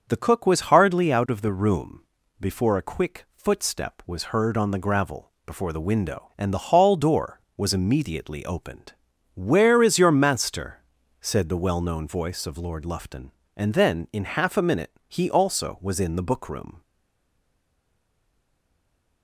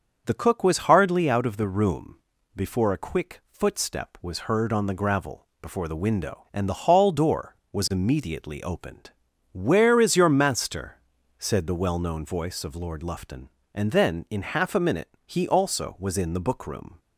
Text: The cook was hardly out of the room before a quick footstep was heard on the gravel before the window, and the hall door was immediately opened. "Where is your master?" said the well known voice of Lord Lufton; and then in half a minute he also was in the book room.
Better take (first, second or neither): second